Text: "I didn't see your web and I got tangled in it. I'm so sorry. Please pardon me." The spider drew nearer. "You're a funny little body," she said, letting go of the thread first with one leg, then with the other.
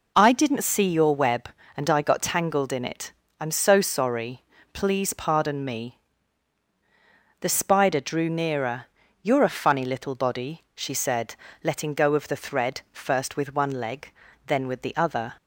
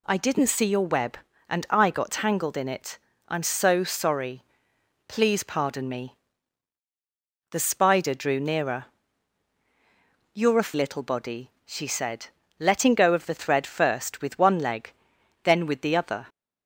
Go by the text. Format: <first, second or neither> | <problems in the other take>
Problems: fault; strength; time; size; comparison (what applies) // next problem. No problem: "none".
first | skips "funny"; at 10.7 s